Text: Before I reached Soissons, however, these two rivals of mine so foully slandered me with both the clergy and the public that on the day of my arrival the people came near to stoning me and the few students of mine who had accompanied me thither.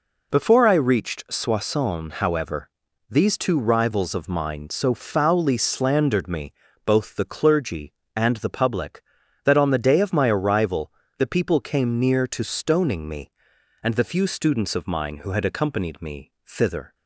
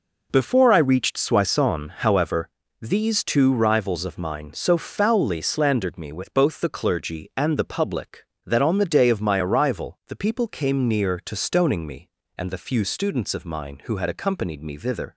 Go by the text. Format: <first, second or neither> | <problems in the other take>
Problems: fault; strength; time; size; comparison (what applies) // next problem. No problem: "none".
second | skips "with"; at 6.6 s // pauses between "arrival" and "the"; slight; at 10.9 s; 0.28 s long // pauses between "me" and "thither"; slight; at 16.3 s; 0.16 s long